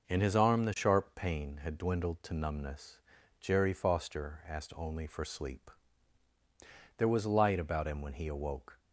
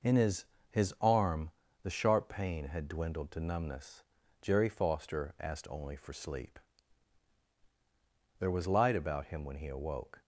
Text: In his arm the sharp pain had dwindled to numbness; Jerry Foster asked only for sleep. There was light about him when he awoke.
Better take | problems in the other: first | says "his" twice; at 0.7 s // pauses between "arm" and "the"; slight; at 1.5 s; 0.32 s long

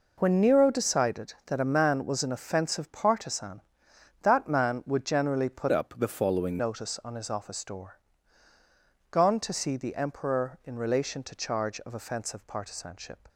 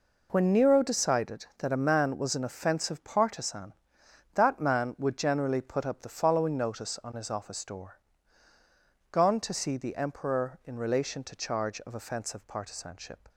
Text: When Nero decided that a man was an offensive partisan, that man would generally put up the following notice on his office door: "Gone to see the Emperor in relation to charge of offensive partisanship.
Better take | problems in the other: second | changes voice from "up" to "following"; from 5.7 to 6.5 s; 0.8 s long

